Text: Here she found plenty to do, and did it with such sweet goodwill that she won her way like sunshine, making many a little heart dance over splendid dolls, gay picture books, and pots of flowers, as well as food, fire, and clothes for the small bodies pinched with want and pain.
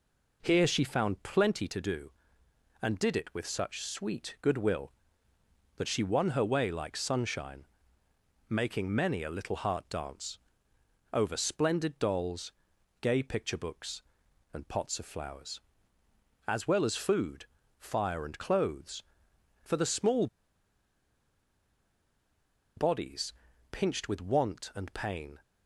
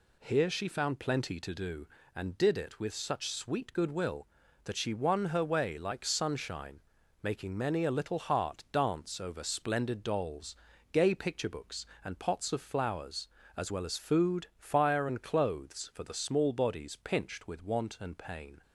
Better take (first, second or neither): second